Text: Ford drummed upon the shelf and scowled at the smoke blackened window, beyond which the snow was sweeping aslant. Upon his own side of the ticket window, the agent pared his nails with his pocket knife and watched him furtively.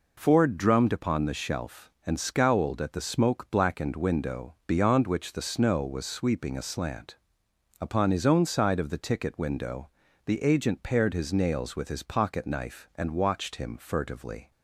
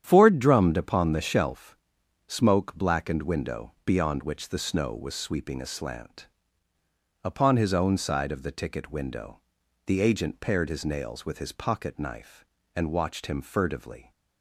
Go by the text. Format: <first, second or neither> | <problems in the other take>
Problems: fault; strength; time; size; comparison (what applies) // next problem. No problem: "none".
first | starts louder than the rest; strong; until 1.0 s; 9 dB // skips "and scowled at the"; at 2.0 s